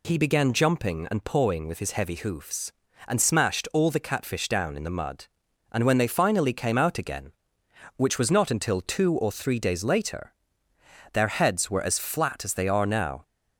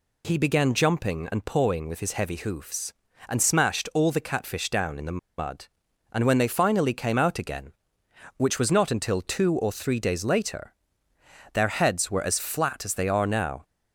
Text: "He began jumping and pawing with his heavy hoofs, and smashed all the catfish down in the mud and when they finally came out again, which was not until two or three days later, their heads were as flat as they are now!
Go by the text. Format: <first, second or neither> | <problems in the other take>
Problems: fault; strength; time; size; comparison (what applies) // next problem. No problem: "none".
first | pauses between "the" and "mud"; slight; at 5.1 s; 0.18 s long